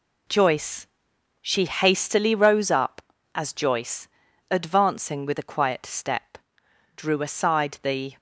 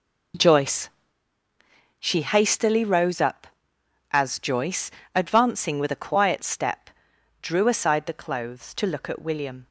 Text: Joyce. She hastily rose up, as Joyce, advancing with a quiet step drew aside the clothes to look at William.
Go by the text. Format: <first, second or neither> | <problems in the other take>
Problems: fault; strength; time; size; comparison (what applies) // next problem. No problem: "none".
second | pauses between "step" and "drew"; noticeable; at 6.2 s; 0.72 s long; noticeable in the second // stops before "clothes to look at William"; at 8.1 s